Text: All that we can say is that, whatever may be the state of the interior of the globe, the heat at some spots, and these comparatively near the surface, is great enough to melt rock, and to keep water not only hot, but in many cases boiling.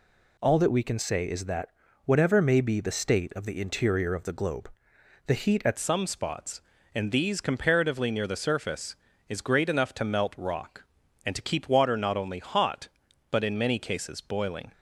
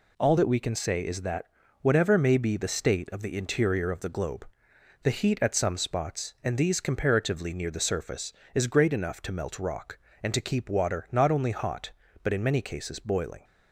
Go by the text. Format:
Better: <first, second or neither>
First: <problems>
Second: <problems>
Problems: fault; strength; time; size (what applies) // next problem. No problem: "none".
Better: second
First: changes voice at "some"; from 5.7 s on; 9.0 s long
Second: none